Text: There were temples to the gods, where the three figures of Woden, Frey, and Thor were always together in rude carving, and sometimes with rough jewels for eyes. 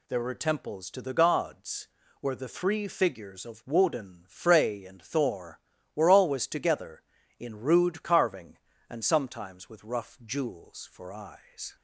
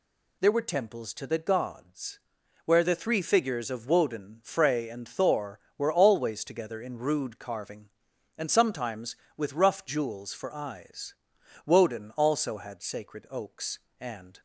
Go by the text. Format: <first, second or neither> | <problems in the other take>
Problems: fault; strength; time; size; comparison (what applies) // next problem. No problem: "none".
first | goes on to say "Woden also had sacred oaks and"; strong; from 11.6 s on; 2.7 s long